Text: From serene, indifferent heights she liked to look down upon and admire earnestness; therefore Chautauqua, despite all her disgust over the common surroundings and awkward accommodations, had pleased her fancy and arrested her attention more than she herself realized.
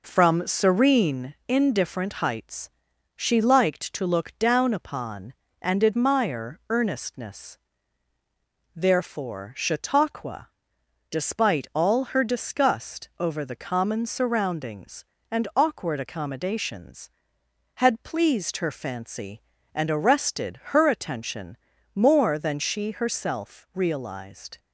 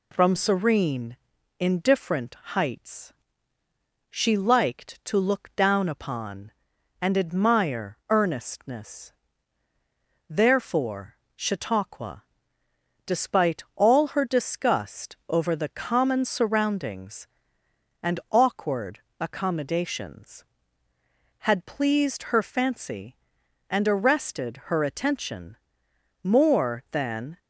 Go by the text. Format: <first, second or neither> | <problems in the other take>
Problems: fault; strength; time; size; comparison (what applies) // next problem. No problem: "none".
first | pauses between "indifferent" and "heights"; slight; at 2.3 s; 0.16 s long // pauses between "heights" and "she"; noticeable; at 3.1 s; 0.96 s long; noticeable in the first // pauses between "therefore" and "Chautauqua"; slight; at 11.1 s; 0.18 s long // pauses between "awkward" and "accommodations"; slight; at 18.9 s; 0.20 s long // pauses between "attention" and "more"; noticeable; at 25.5 s; 0.66 s long; also in the first // stops before "she herself realized"; at 27.3 s